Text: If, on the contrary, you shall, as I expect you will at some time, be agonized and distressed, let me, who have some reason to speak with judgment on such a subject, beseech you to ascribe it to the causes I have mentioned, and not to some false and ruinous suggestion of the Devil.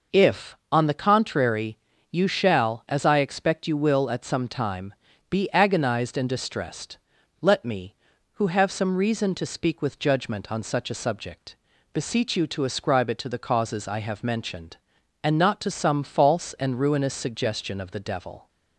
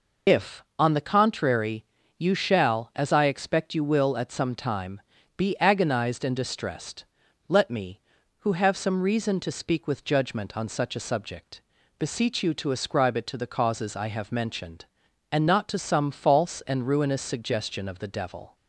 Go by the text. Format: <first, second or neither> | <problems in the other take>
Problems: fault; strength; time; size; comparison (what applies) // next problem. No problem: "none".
first | loses the start of "If"; at 0.2 s; 80 ms